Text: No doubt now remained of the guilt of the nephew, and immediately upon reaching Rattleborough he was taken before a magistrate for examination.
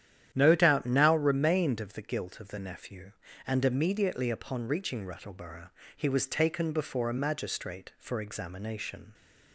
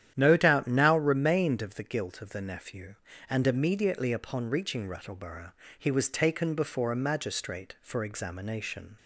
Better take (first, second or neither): neither